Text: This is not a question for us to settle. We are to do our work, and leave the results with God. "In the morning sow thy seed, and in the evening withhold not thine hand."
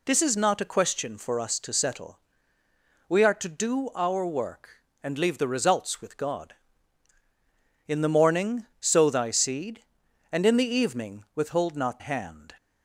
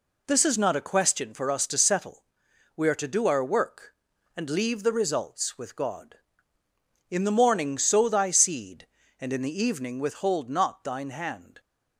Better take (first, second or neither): second